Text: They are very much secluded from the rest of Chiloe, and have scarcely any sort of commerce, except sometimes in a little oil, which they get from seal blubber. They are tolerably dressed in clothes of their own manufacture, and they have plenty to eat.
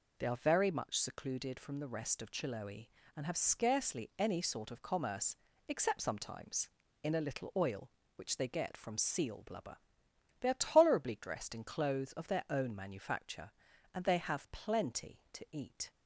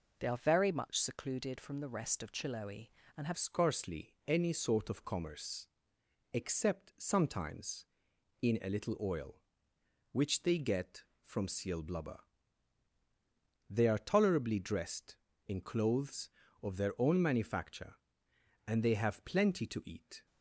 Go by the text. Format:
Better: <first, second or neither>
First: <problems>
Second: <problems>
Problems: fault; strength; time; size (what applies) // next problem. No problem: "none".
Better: first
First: none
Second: changes voice at "scarcely"; from 3.3 s on; 16.9 s long